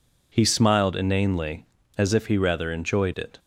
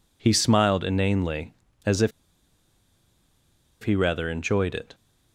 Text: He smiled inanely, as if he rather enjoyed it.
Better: first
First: none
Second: pauses between "if" and "he"; strong; at 2.1 s; 1.7 s long

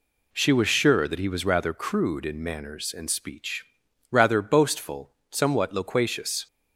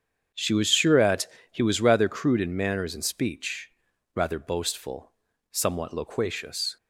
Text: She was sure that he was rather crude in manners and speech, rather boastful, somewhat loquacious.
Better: first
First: none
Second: starts louder than the rest; strong; until 1.5 s; 8 dB // says "at" for "that"; at 0.9 s

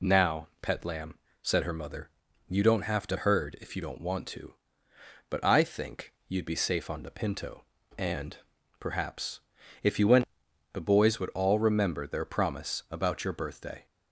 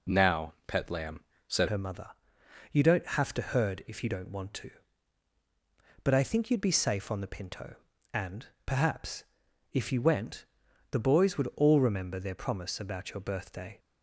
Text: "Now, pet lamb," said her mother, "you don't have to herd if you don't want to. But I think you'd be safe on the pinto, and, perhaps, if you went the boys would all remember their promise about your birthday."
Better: first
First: pauses between "went" and "the"; noticeable; at 10.2 s; 0.46 s long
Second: changes voice at "her"; from 1.6 s on; 12.1 s long // pauses between "went" and "the"; noticeable; at 10.4 s; 0.48 s long

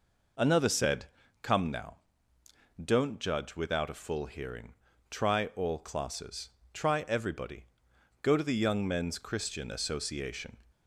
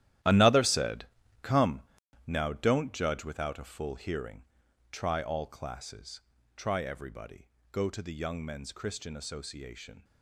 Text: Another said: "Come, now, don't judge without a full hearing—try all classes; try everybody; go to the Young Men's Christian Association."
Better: first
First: none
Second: gets quieter; strong; throughout; 13.5 dB

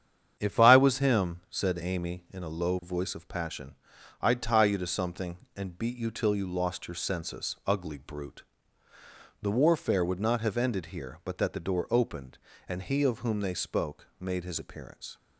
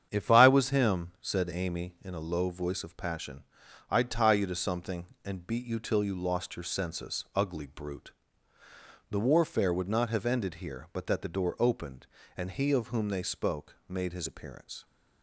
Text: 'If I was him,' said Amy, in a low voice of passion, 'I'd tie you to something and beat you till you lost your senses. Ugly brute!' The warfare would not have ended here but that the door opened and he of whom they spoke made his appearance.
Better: neither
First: starts louder than the rest; strong; until 1.4 s; 8.5 dB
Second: starts louder than the rest; strong; until 1.1 s; 8.5 dB

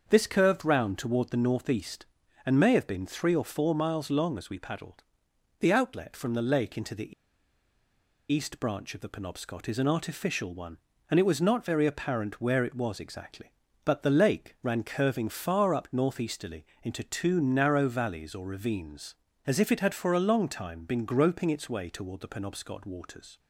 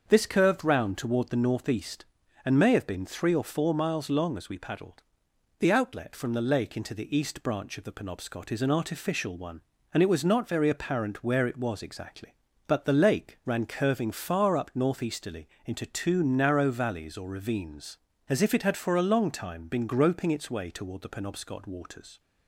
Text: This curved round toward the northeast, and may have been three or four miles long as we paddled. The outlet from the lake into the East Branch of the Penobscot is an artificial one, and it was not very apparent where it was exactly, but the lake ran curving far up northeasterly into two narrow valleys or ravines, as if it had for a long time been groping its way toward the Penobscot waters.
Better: second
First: starts louder than the rest; until 1.0 s; 7 dB // pauses between "the" and "East"; at 7.1 s; 1.1 s long // pauses between "northeasterly" and "into"; slight; at 16.6 s; 0.18 s long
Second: starts louder than the rest; until 1.0 s; 6.5 dB // pauses between "northeasterly" and "into"; slight; at 15.4 s; 0.18 s long

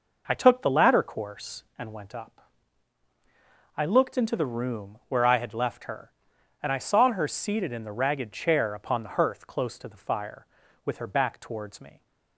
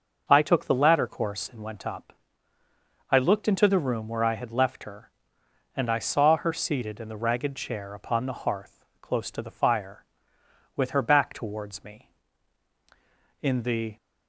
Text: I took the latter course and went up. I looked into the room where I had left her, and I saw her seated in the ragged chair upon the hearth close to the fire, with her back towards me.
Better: first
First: none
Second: starts louder than the rest; until 1.3 s; 6 dB // pauses between "hearth" and "close"; slight; at 8.8 s; 0.16 s long // goes on to say "In the"; from 13.4 s on; 0.56 s long

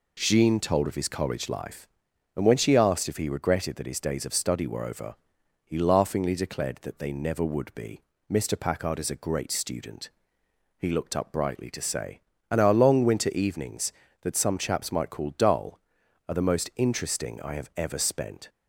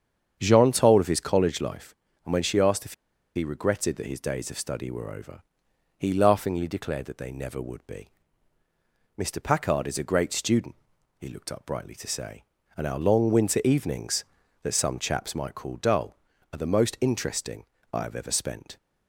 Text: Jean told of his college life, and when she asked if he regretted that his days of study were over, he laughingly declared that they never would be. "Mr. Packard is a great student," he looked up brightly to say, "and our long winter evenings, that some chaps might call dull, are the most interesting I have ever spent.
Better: first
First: none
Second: starts louder than the rest; strong; until 1.4 s; 8 dB // pauses between "if" and "he"; at 2.9 s; 0.42 s long // pauses between "interesting" and "I"; slight; at 17.6 s; 0.28 s long

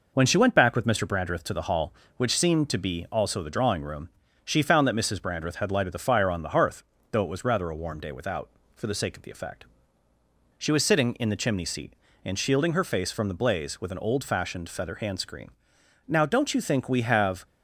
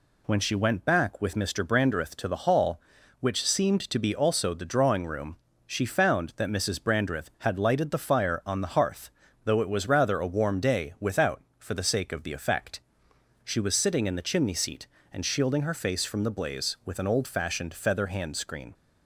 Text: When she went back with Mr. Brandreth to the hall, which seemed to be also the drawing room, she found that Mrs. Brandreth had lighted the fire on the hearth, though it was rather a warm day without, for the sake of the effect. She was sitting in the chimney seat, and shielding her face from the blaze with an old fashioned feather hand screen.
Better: second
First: goes on to say "Now don't you think we have"; from 16.0 s on; 1.3 s long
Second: none

